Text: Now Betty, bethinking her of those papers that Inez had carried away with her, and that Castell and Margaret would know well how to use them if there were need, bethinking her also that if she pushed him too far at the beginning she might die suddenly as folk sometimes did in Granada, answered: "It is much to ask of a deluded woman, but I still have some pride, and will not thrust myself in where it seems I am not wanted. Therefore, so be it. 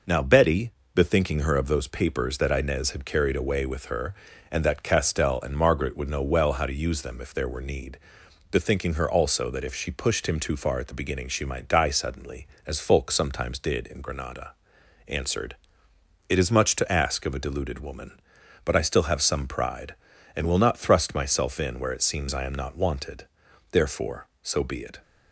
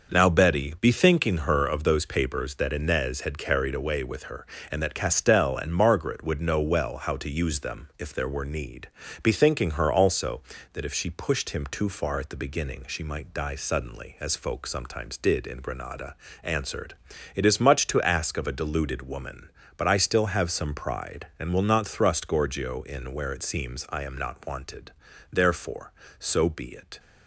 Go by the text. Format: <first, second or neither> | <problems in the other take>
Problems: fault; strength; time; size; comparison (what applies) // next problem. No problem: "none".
first | starts louder than the rest; until 1.1 s; 6 dB // says "gorgio" for "myself"; at 22.2 s